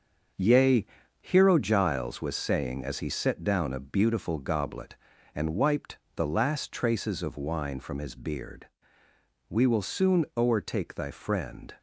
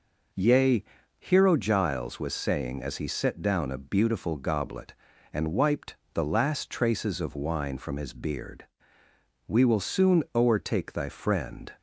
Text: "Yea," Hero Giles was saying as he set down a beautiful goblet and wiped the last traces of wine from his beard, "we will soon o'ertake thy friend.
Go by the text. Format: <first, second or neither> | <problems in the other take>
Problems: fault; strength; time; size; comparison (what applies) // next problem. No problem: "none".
second | gets quieter; strong; throughout; 7.5 dB // pauses between "wiped" and "the"; slight; at 5.9 s; 0.18 s long; slight in the second